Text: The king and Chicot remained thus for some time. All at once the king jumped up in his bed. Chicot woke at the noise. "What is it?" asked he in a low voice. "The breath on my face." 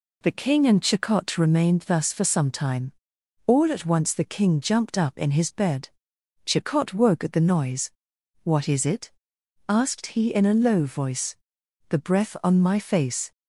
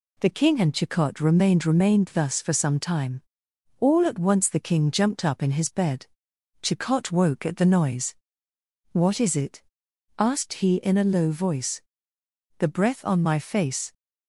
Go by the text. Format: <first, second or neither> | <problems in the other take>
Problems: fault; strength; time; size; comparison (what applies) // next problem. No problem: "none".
first | says "remained" twice; at 1.6 s